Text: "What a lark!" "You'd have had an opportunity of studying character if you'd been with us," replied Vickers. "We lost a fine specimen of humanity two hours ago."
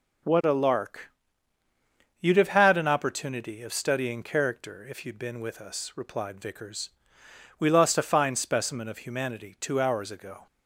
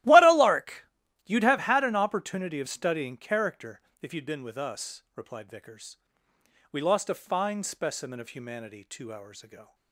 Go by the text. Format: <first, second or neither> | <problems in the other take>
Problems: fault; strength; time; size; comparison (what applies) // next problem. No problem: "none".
first | starts louder than the rest; strong; until 1.6 s; 15 dB // pauses between "character" and "if"; slight; at 3.8 s; 0.20 s long